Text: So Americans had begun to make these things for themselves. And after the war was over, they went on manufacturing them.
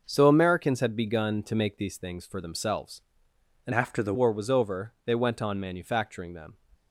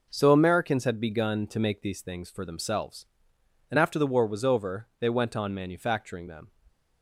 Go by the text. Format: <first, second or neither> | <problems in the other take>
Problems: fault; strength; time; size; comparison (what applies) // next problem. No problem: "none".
second | changes voice from "after" to "the"; from 3.7 to 4.1 s; 0.4 s long